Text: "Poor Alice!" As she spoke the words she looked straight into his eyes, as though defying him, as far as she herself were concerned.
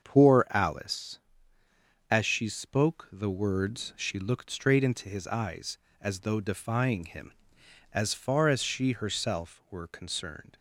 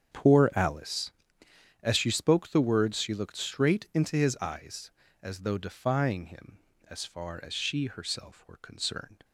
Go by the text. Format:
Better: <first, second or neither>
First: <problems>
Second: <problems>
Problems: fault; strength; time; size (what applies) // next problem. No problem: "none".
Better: neither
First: starts louder than the rest; until 1.0 s; 7 dB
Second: starts louder than the rest; strong; until 1.8 s; 8 dB